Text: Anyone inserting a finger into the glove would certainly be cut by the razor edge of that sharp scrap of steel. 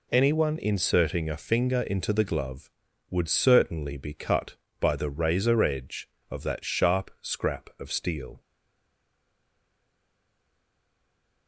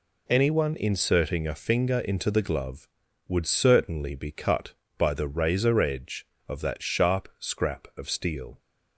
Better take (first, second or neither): second